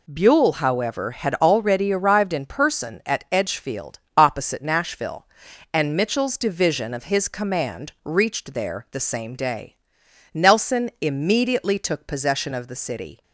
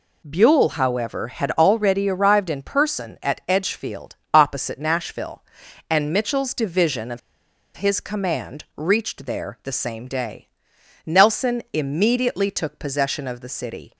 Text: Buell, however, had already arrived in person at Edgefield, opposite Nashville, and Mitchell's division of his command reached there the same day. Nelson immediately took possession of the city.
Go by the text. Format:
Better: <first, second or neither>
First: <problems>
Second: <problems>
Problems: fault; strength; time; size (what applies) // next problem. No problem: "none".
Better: first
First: none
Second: pauses between "of" and "his"; noticeable; at 7.1 s; 0.57 s long